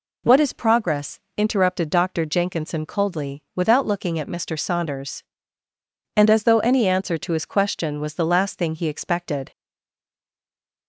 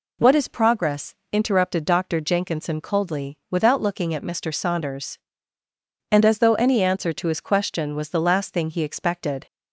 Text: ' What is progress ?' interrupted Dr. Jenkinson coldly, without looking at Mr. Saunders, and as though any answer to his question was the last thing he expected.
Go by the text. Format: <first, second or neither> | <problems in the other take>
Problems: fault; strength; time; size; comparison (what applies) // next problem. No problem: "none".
second | stays silent after the last word; noticeable; from 9.5 s on; 1.3 s long